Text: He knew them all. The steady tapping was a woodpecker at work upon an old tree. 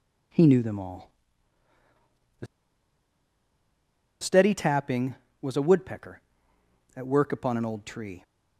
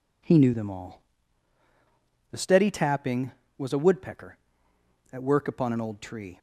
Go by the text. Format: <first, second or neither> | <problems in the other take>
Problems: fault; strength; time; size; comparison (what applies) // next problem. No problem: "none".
second | pauses between "The" and "steady"; strong; at 2.4 s; 1.7 s long